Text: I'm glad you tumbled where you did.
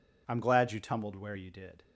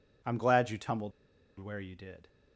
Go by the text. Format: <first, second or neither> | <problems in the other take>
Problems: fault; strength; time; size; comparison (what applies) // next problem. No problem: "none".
first | pauses between "tumbled" and "where"; noticeable; at 1.1 s; 0.48 s long